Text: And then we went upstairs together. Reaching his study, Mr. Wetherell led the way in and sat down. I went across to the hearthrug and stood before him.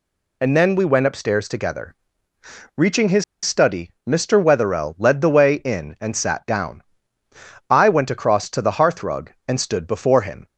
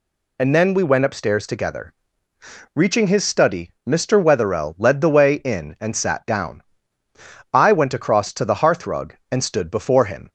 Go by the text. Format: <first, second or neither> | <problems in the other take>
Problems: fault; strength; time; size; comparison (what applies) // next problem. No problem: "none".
second | pauses between "his" and "study"; slight; at 3.2 s; 0.19 s long